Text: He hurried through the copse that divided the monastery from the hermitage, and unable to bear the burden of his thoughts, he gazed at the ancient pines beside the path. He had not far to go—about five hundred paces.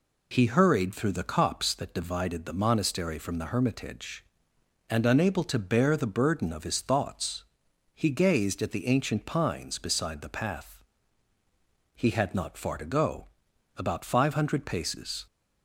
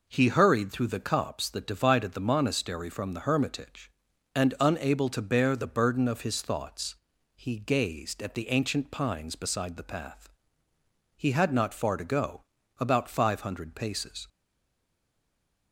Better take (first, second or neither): first